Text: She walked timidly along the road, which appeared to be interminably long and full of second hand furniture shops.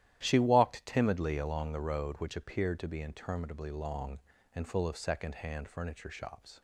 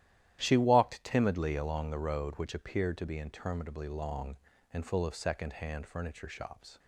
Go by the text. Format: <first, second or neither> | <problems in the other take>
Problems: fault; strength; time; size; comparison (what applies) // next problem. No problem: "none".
neither | starts louder than the rest; strong; the same in both